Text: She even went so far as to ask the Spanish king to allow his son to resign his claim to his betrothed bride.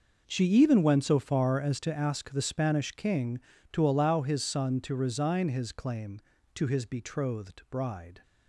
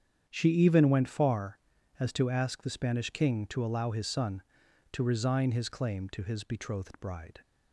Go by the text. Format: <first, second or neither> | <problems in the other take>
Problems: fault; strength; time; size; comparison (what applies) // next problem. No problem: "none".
first | starts louder than the rest; strong; until 1.2 s; 8.5 dB // skips "so"; at 1.0 s